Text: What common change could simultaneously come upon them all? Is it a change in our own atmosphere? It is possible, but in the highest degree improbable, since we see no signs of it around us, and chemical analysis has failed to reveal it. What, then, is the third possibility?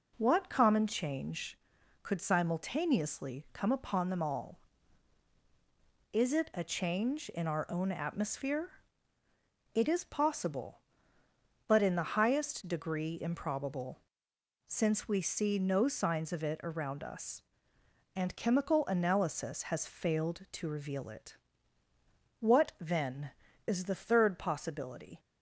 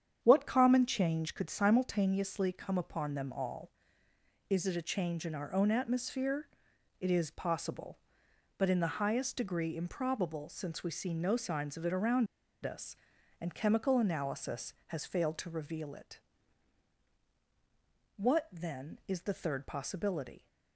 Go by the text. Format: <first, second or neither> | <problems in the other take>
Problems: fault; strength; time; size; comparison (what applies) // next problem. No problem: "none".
first | starts louder than the rest; strong; until 1.2 s; 8.5 dB // pauses between "around" and "us"; at 12.2 s; 0.38 s long